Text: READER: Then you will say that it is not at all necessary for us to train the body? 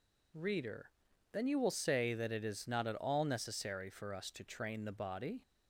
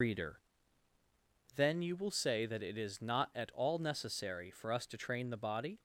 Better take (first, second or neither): first